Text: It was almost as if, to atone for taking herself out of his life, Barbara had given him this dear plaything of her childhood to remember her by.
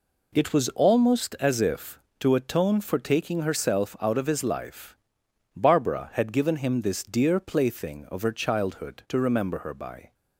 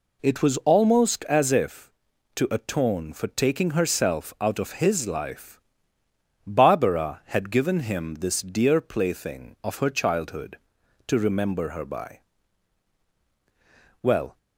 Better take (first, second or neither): first